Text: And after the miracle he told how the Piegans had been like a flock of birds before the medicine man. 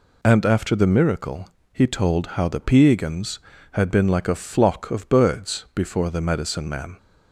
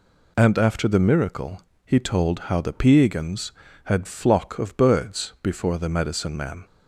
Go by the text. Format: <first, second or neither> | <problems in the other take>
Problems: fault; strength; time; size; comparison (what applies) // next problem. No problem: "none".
first | pauses between "miracle" and "he"; slight; at 1.6 s; 0.24 s long; slight in the first // skips "been like a"; at 4.0 s